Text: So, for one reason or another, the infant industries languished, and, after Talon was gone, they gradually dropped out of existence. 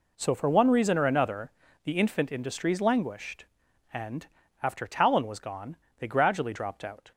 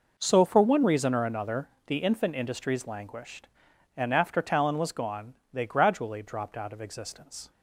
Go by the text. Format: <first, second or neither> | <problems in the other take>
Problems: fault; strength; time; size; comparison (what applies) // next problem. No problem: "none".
second | stops before "of existence"; at 7.1 s